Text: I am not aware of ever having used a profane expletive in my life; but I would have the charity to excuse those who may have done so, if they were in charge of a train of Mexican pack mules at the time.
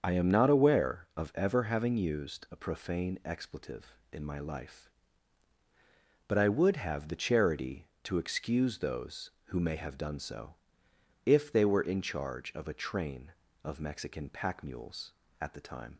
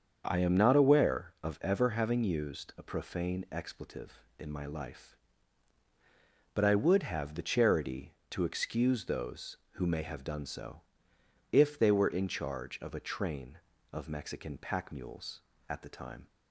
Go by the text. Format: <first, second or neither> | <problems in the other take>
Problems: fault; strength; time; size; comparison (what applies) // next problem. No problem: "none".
second | loses the start of "I"; at 0.0 s; 60 ms // starts louder than the rest; until 1.0 s; 7 dB; also in the second